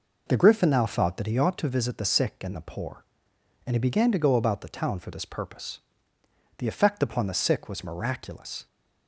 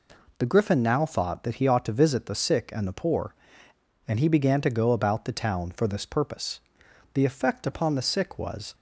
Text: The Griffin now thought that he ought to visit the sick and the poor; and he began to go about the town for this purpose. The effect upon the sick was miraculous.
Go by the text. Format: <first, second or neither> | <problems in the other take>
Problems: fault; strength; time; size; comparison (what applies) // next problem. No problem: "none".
first | stops before "miraculous"; at 8.7 s